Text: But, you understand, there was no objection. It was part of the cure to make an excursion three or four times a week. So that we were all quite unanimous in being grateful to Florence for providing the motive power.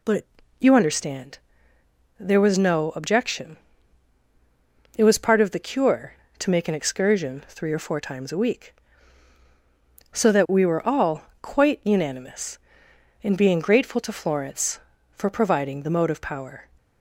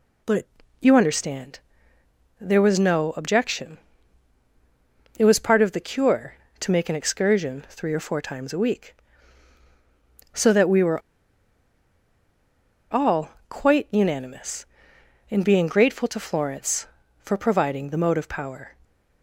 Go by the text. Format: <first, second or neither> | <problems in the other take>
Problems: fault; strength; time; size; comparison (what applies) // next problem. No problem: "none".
first | pauses between "were" and "all"; strong; at 11.0 s; 1.9 s long // pauses between "all" and "quite"; slight; at 13.3 s; 0.18 s long; slight in the first